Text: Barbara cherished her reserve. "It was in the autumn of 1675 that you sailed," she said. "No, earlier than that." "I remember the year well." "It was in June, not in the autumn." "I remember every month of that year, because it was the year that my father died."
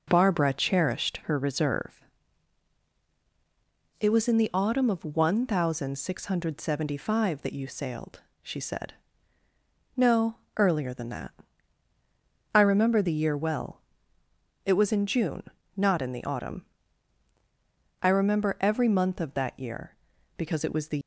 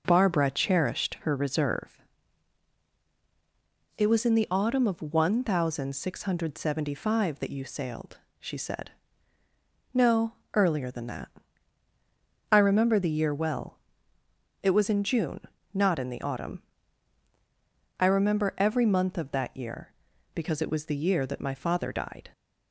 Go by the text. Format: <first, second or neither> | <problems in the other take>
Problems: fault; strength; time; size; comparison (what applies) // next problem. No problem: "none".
second | stops before "year that my father died"; at 21.0 s